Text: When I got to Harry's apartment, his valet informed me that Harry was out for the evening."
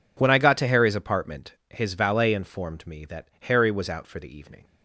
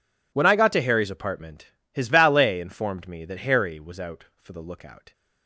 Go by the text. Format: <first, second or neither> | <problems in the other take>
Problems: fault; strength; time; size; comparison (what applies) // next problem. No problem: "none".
first | says "lookout" for "evening"; at 4.6 s